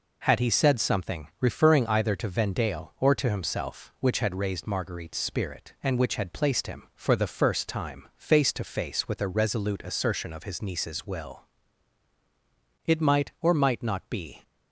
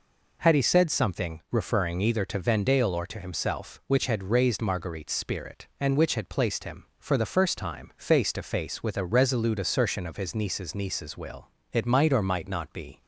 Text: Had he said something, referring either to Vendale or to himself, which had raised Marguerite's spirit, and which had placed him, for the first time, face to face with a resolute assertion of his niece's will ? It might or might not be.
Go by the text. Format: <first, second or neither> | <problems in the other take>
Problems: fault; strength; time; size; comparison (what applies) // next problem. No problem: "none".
first | says "niece's" twice; at 10.7 s